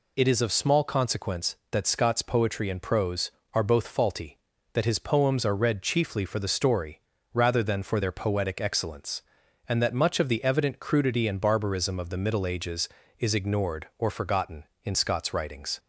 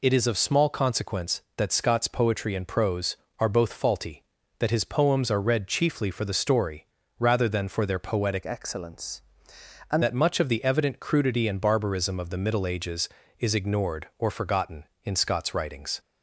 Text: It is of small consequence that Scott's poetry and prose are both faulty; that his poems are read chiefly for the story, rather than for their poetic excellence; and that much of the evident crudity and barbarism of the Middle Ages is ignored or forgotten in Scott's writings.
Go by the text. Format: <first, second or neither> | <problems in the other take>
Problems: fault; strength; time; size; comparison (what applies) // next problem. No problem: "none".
first | changes voice from "excellence" to "and"; from 8.4 to 10.0 s; 1.6 s long